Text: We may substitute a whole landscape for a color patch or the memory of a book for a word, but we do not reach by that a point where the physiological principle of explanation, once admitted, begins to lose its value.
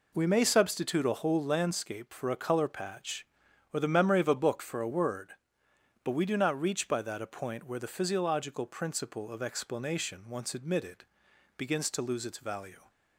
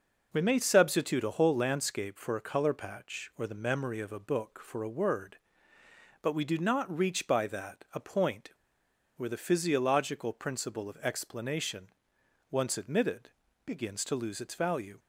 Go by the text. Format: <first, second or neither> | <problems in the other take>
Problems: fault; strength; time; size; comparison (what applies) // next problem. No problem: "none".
first | pauses between "point" and "where"; noticeable; at 8.5 s; 0.65 s long